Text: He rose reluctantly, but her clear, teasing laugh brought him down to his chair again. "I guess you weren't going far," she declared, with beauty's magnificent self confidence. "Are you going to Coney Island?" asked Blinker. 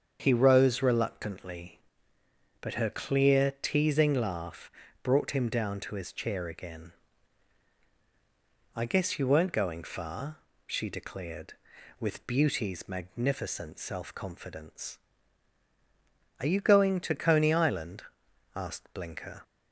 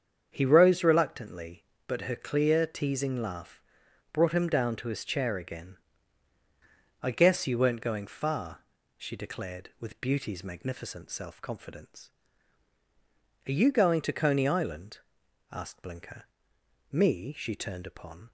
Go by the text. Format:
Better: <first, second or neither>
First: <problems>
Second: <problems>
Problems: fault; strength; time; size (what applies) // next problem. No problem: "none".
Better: first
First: starts louder than the rest; strong; until 1.2 s; 7 dB // pauses between "laugh" and "brought"; slight; at 4.6 s; 0.32 s long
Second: starts louder than the rest; strong; until 1.3 s; 7.5 dB // pauses between "laugh" and "brought"; noticeable; at 3.6 s; 0.52 s long // goes on to say "Me She turned upon"; from 16.9 s on; 1.4 s long